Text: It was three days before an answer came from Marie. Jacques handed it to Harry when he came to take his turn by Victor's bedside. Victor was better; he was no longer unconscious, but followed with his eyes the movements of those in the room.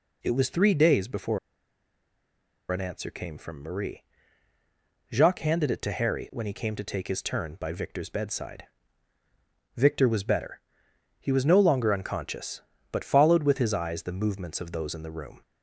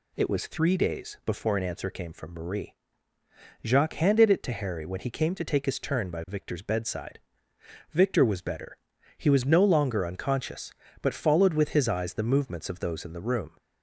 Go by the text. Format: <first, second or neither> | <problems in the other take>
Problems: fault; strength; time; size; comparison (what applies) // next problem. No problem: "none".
second | pauses between "before" and "an"; strong; at 1.3 s; 1.3 s long